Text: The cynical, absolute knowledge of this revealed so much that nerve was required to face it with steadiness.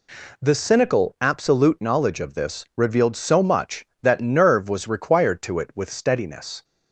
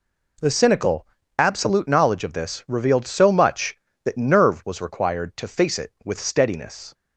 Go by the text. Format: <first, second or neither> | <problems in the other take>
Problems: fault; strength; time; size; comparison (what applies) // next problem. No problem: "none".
second | skips "face"; at 5.5 s